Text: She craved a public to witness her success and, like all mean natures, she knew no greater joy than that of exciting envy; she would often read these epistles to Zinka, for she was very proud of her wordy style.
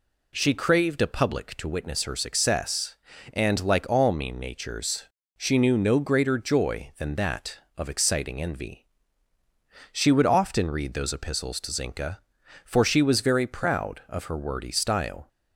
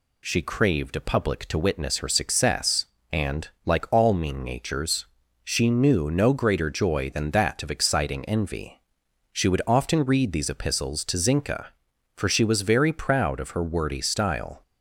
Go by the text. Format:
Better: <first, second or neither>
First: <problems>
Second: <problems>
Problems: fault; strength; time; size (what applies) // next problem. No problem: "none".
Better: second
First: says "those" for "these"; at 10.9 s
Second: none